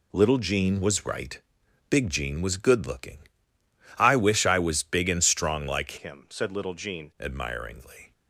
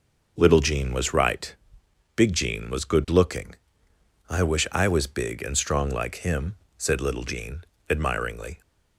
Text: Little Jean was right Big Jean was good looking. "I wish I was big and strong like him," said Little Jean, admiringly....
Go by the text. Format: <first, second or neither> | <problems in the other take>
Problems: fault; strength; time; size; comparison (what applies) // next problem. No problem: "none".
second | pauses between "right" and "Big"; noticeable; at 1.3 s; 0.52 s long; noticeable in the second // changes voice from "him" to "Jean"; from 5.9 to 7.1 s; 1.2 s long